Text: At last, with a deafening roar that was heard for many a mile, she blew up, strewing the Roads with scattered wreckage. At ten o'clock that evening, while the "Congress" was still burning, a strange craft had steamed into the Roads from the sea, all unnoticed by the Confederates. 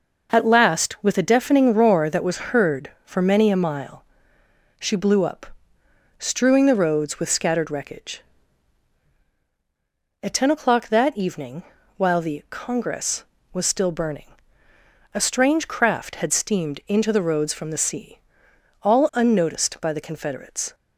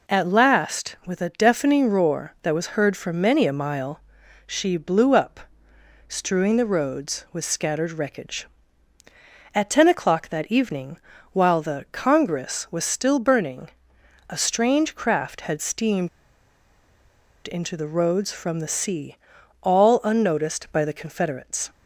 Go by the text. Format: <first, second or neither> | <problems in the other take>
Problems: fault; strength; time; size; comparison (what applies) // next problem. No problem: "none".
first | pauses between "steamed" and "into"; strong; at 16.0 s; 1.3 s long